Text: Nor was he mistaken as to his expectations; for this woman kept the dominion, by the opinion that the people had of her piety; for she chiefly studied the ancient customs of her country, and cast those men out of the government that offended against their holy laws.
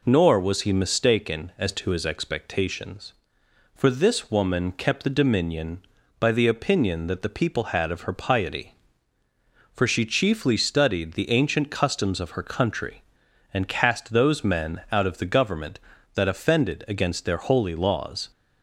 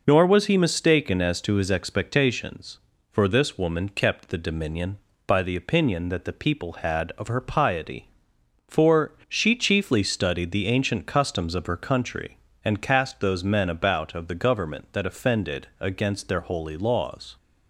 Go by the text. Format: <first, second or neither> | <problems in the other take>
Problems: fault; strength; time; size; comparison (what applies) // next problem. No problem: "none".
first | says "about" for "out"; at 13.7 s